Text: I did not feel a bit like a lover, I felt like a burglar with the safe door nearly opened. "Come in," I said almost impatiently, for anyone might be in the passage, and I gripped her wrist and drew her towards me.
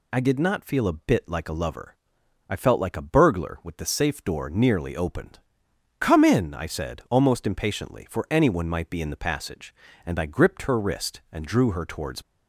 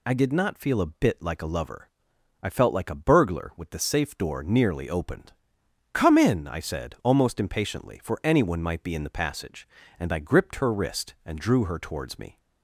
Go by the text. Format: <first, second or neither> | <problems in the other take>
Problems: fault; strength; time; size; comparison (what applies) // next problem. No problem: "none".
second | stops before "me"; at 12.2 s